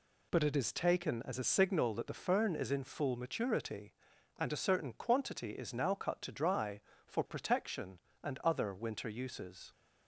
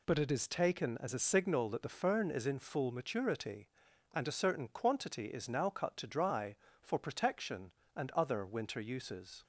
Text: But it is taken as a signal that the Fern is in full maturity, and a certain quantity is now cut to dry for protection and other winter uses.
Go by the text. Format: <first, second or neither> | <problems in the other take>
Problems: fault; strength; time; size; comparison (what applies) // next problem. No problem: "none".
neither | none